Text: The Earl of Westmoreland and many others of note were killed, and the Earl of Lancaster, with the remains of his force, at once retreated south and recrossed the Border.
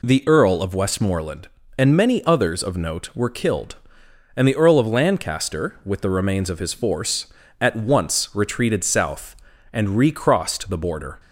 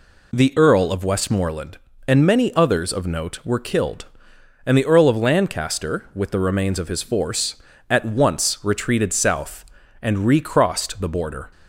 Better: neither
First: none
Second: none

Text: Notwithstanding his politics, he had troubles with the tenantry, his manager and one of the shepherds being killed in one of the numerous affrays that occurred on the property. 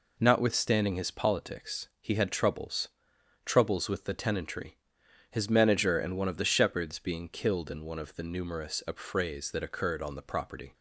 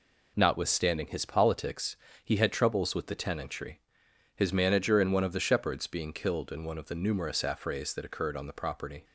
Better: second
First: says "troubles" twice; at 3.4 s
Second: none

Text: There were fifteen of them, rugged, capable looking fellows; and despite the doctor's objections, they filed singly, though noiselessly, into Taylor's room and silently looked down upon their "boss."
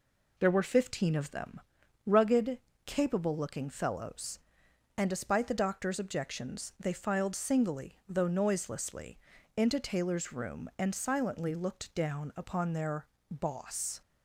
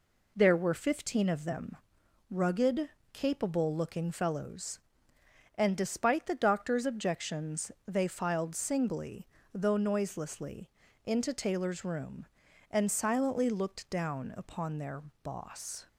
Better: neither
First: pauses between "their" and "boss"; slight; at 13.0 s; 0.24 s long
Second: pauses between "their" and "boss"; slight; at 15.0 s; 0.22 s long

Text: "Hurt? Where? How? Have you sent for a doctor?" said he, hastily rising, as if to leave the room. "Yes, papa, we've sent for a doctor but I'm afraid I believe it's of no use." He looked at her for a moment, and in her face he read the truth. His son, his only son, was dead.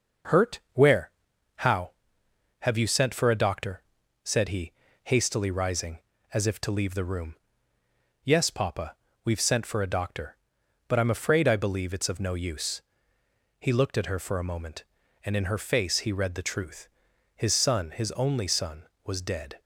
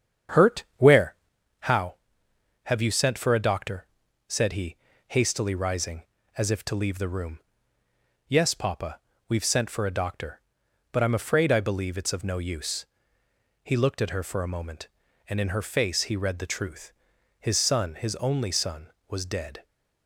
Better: first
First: none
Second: starts louder than the rest; strong; until 1.4 s; 8.5 dB

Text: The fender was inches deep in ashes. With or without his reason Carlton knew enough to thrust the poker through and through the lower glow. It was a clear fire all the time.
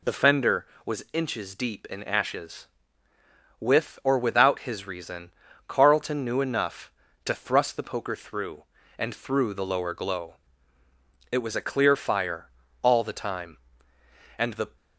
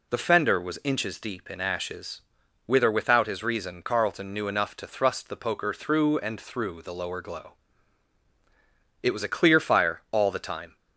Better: second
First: pauses between "reason" and "Carlton"; at 5.2 s; 0.38 s long // pauses between "fire" and "all"; slight; at 12.4 s; 0.36 s long // goes on to say "And the"; slight; from 14.3 s on; 0.38 s long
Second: none

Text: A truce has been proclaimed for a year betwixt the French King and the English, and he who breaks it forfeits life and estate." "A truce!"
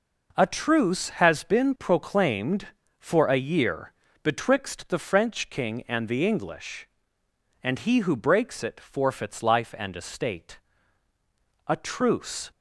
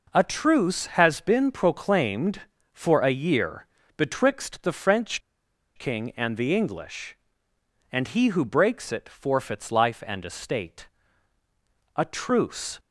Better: first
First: pauses between "year" and "betwixt"; slight; at 3.9 s; 0.32 s long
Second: pauses between "year" and "betwixt"; slight; at 3.6 s; 0.32 s long // pauses between "French" and "King"; noticeable; at 5.2 s; 0.56 s long

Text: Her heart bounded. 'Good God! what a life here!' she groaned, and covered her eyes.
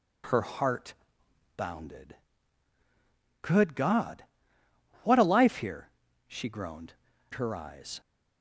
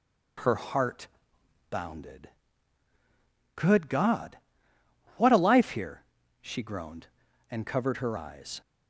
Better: second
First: pauses between "heart" and "bounded"; noticeable; at 0.9 s; 0.60 s long // skips "and covered"; at 7.1 s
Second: pauses between "heart" and "bounded"; noticeable; at 1.0 s; 0.60 s long

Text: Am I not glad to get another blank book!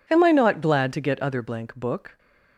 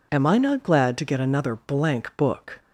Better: second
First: says "other" for "another"; at 1.2 s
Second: none

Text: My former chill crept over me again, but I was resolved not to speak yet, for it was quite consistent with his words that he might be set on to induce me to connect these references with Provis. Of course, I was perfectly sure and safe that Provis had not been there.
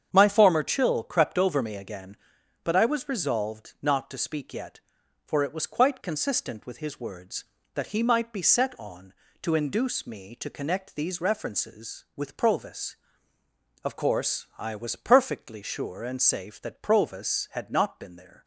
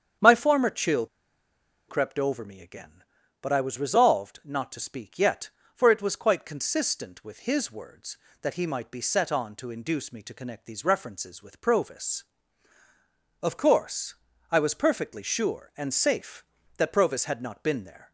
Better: first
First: starts louder than the rest; strong; until 1.1 s; 8 dB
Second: starts louder than the rest; strong; until 2.0 s; 8 dB // pauses between "chill" and "crept"; noticeable; at 1.0 s; 0.81 s long

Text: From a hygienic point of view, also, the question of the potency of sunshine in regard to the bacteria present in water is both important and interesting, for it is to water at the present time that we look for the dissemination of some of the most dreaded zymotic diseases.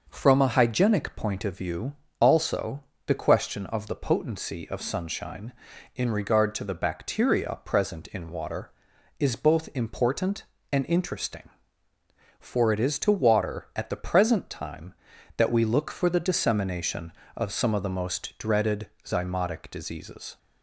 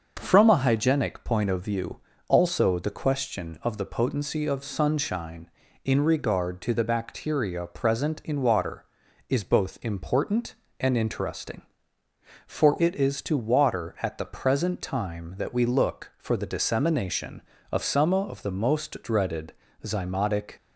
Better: first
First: pauses between "dreaded" and "zymotic"; slight; at 18.8 s; 0.16 s long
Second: starts louder than the rest; until 1.2 s; 6.5 dB // pauses between "dreaded" and "zymotic"; slight; at 19.5 s; 0.28 s long // stops before "diseases"; at 20.5 s

